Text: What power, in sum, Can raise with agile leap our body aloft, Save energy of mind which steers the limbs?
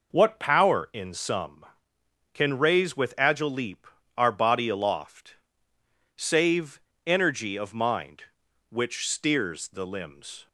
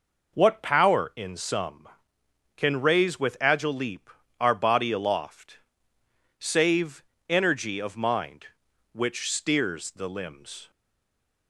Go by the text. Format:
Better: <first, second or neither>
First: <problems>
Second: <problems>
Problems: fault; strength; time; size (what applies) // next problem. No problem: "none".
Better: first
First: pauses between "leap" and "our"; slight; at 3.8 s; 0.30 s long // pauses between "Save" and "energy"; slight; at 6.8 s; 0.24 s long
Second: pauses between "leap" and "our"; slight; at 4.1 s; 0.30 s long // pauses between "Save" and "energy"; slight; at 7.0 s; 0.24 s long // stays silent after the last word; slight; from 10.7 s on; 0.7 s long